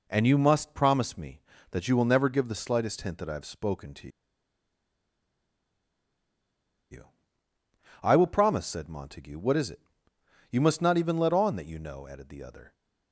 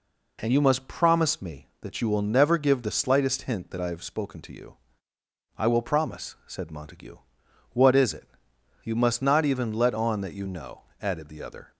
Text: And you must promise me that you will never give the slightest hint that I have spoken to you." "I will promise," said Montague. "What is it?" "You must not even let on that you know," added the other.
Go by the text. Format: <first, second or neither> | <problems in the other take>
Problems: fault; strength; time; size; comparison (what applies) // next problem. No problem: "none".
second | pauses between "to" and "you"; strong; at 4.0 s; 2.8 s long